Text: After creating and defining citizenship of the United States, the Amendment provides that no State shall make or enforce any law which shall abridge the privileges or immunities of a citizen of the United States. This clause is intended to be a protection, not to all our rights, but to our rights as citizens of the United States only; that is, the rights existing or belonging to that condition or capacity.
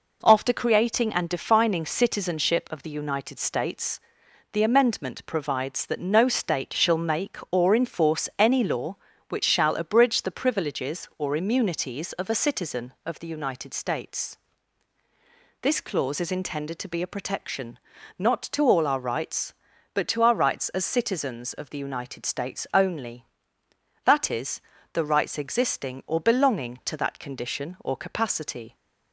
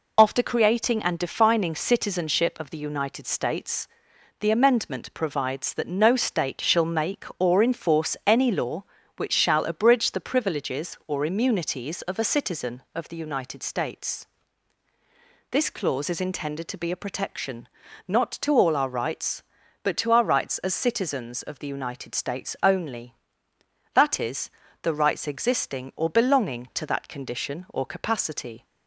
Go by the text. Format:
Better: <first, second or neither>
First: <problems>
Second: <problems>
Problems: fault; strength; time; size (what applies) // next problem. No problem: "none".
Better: first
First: none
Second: loses the start of "After"; at 0.1 s; 65 ms